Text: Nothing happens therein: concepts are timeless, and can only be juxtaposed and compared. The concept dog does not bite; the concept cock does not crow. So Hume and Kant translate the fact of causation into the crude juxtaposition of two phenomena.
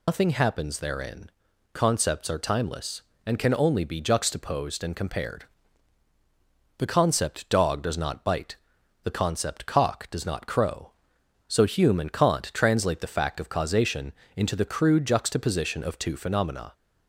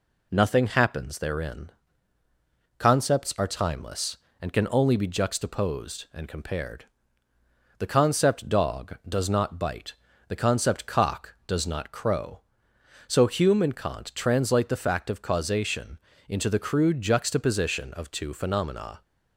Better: second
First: loses the start of "Nothing"; at 0.0 s; 105 ms // pauses between "causation" and "into"; slight; at 14.1 s; 0.24 s long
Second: pauses between "causation" and "into"; slight; at 15.9 s; 0.32 s long

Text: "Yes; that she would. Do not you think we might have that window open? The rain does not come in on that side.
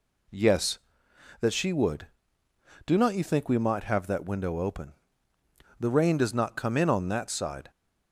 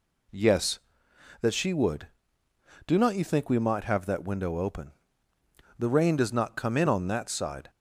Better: neither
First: none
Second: none

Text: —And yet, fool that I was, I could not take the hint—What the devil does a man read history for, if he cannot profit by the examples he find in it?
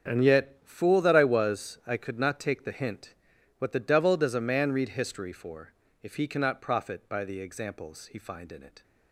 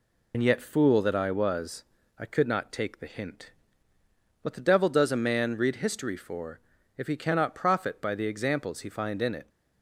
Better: first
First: none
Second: loses the start of "And"; at 0.3 s; 70 ms

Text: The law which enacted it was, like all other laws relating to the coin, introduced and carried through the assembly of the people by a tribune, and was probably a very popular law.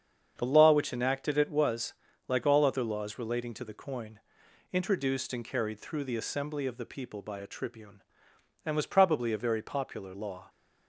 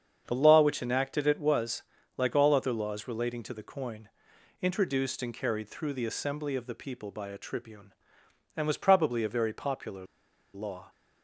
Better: first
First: starts louder than the rest; strong; until 1.3 s; 7.5 dB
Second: starts louder than the rest; strong; until 1.2 s; 7.5 dB // pauses between "popular" and "law"; noticeable; at 10.0 s; 0.49 s long

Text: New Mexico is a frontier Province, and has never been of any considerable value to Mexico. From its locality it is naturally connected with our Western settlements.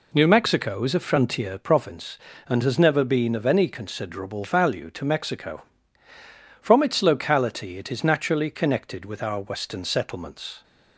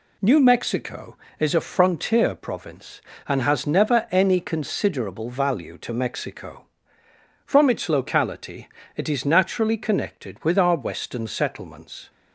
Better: first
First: none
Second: skips "been of"; at 4.0 s // pauses between "locality" and "it"; slight; at 8.6 s; 0.28 s long

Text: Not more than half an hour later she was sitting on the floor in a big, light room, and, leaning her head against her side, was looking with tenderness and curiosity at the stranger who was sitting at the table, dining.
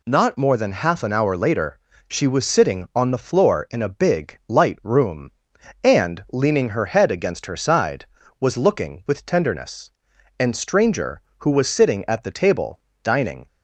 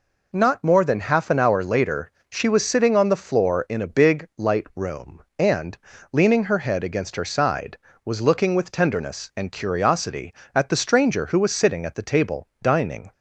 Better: second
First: pauses between "later" and "she"; slight; at 1.7 s; 0.30 s long // skips "curiosity at the"; at 10.5 s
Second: pauses between "later" and "she"; slight; at 2.0 s; 0.22 s long

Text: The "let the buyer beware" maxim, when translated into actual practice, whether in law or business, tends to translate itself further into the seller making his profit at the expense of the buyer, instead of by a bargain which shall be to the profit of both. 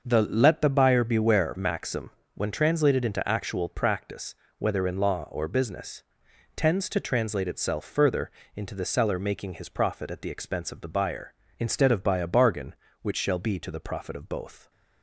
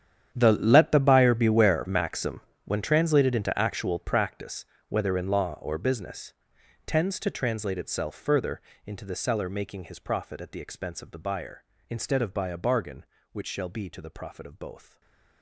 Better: first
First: starts louder than the rest; noticeable; until 1.0 s; 6 dB // pauses between "further" and "into"; slight; at 8.3 s; 0.24 s long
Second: gets quieter; strong; throughout; 17.5 dB // starts louder than the rest; strong; until 1.3 s; 9 dB // pauses between "further" and "into"; slight; at 8.6 s; 0.24 s long // stays silent after the last word; slight; from 14.8 s on; 0.6 s long

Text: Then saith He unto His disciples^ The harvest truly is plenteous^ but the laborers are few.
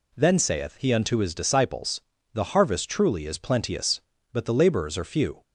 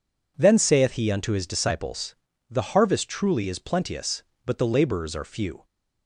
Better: neither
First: pauses between "disciples" and "The"; slight; at 2.0 s; 0.32 s long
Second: pauses between "disciples" and "The"; slight; at 2.1 s; 0.34 s long

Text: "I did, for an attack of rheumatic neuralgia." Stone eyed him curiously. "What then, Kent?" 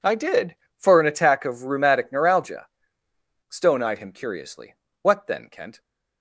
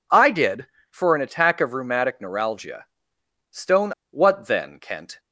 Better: first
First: none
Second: skips "eyed him curiously"; at 4.0 s

